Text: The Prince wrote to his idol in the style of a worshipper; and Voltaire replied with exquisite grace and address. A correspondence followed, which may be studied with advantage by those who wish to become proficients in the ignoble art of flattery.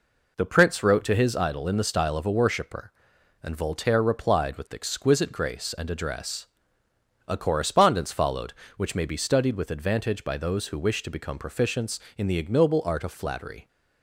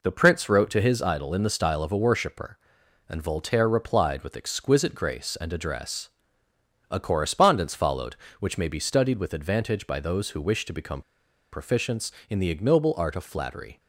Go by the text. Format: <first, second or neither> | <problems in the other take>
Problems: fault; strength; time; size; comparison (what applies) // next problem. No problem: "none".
first | pauses between "become" and "proficients"; noticeable; at 11.0 s; 0.50 s long